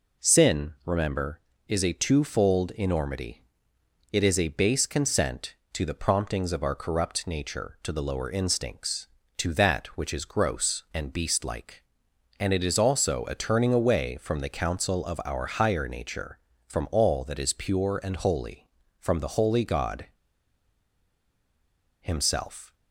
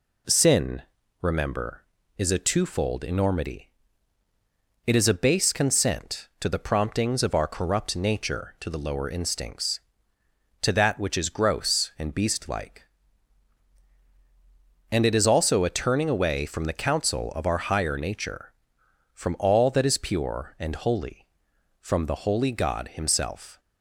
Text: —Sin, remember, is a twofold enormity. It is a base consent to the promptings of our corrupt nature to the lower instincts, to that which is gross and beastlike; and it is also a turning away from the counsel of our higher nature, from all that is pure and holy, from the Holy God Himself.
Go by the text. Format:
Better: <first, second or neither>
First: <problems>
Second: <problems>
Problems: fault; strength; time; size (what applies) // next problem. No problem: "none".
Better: second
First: pauses between "God" and "Himself"; strong; at 20.0 s; 1.9 s long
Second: none